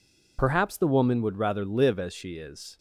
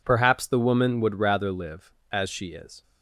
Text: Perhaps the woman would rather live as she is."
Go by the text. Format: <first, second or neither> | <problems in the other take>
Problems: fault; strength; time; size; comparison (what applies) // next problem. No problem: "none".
second | loses the start of "Perhaps"; at 0.3 s; 20 ms